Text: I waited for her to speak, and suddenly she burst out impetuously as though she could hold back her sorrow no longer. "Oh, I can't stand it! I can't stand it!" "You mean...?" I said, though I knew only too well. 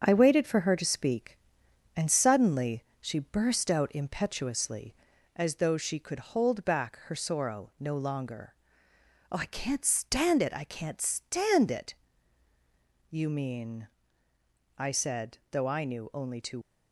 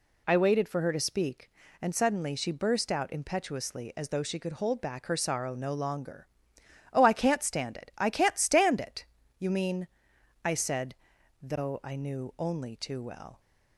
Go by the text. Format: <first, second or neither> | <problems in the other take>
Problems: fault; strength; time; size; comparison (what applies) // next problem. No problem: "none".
second | starts louder than the rest; strong; until 1.0 s; 7 dB // pauses between "suddenly" and "she"; slight; at 2.8 s; 0.18 s long // stops before "well"; at 16.6 s